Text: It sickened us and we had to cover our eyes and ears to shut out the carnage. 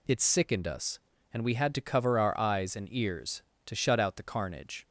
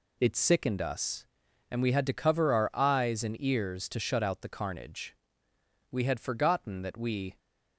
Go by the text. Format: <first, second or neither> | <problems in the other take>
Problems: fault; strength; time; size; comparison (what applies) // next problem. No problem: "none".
first | goes on to say "We had forgotten that we"; from 5.9 s on; 1.4 s long